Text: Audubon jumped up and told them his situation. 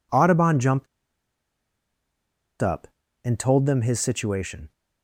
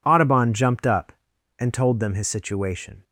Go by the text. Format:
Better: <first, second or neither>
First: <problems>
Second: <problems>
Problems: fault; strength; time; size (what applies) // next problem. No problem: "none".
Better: second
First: pauses between "jumped" and "up"; strong; at 0.8 s; 1.7 s long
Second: none